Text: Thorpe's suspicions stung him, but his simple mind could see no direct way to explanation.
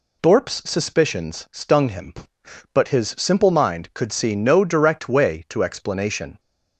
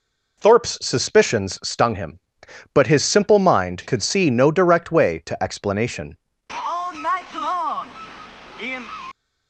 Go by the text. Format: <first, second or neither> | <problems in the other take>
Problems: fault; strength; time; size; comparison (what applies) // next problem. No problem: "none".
first | goes on to say "All night long in"; strong; from 6.5 s on; 2.4 s long